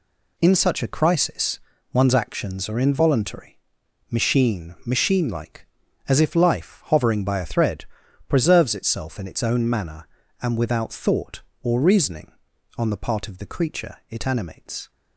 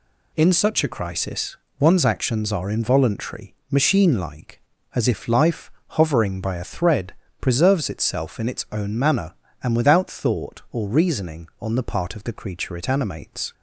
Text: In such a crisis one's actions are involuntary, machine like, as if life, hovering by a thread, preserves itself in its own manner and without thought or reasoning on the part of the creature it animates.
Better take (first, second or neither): second